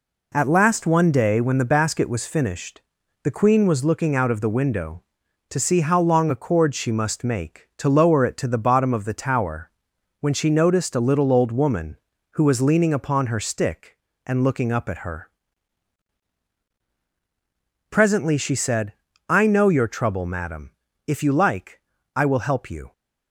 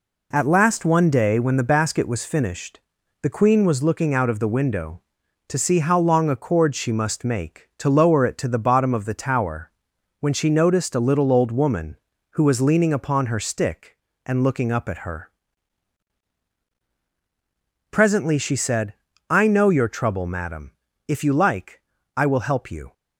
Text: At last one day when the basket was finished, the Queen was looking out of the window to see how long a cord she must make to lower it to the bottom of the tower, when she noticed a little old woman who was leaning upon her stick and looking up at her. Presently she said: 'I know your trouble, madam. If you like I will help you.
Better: neither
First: pauses between "like" and "I"; slight; at 21.8 s; 0.34 s long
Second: pauses between "like" and "I"; slight; at 21.8 s; 0.34 s long

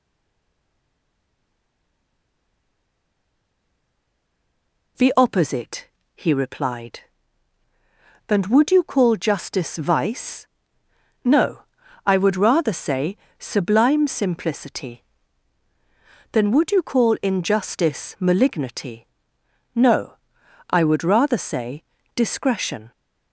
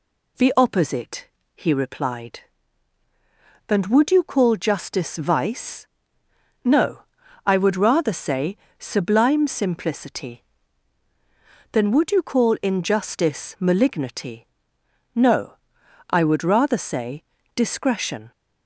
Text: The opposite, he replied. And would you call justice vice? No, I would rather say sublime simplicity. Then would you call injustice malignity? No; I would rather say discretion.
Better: second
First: stays silent before the first word; strong; until 4.9 s; 4.9 s long // pauses between "say" and "sublime"; slight; at 13.1 s; 0.20 s long // pauses between "say" and "discretion"; slight; at 21.8 s; 0.32 s long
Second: pauses between "say" and "sublime"; slight; at 8.5 s; 0.20 s long // pauses between "say" and "discretion"; slight; at 17.2 s; 0.32 s long

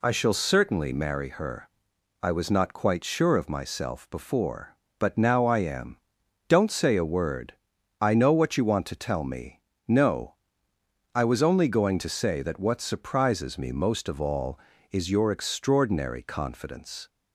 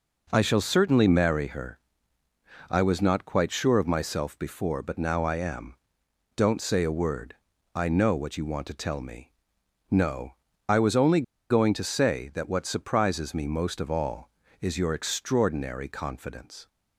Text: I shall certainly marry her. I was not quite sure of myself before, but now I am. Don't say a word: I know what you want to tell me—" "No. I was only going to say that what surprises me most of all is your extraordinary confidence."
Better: first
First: none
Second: pauses between "only" and "going"; slight; at 11.2 s; 0.27 s long

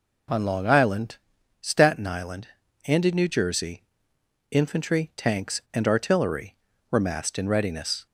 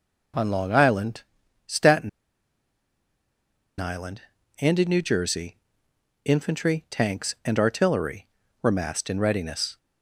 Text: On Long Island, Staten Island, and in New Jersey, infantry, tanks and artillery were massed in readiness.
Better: first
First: none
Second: pauses between "Staten" and "Island"; strong; at 2.0 s; 1.6 s long

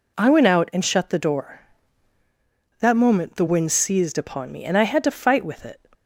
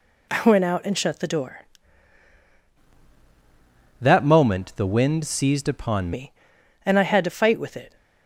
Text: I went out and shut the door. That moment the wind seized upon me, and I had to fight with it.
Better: first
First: none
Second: changes voice from "That" to "upon"; from 4.0 to 6.1 s; 2.1 s long

